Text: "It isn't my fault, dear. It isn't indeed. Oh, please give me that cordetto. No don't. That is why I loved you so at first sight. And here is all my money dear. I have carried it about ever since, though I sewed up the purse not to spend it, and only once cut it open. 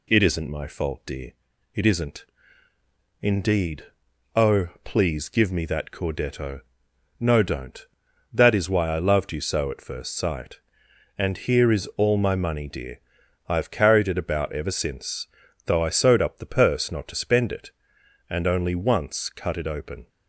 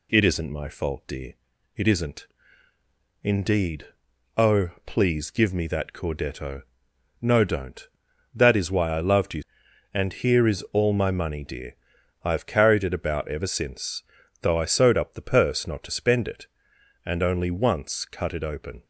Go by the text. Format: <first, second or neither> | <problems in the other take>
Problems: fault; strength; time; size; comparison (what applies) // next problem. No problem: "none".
first | pauses between "isn't" and "indeed"; noticeable; at 2.2 s; 0.96 s long; noticeable in the first // skips "so at first sight"; at 9.6 s